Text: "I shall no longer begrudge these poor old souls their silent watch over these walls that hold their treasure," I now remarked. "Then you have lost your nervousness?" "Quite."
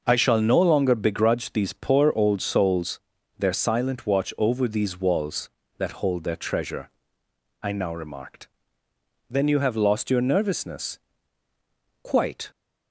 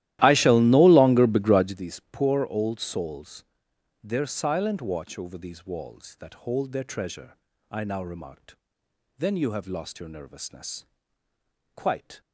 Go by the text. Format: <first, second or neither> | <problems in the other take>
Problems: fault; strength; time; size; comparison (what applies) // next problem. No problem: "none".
first | starts louder than the rest; strong; until 1.8 s; 14.5 dB // pauses between "souls" and "their"; noticeable; at 3.4 s; 0.62 s long; also in the first